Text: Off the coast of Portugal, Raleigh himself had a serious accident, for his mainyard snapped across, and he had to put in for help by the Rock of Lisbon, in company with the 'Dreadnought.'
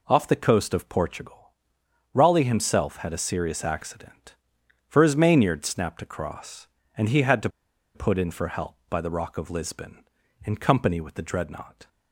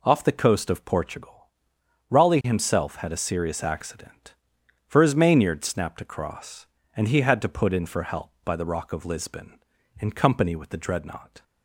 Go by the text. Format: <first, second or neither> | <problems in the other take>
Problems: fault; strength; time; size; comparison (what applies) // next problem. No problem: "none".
second | pauses between "to" and "put"; noticeable; at 7.4 s; 0.46 s long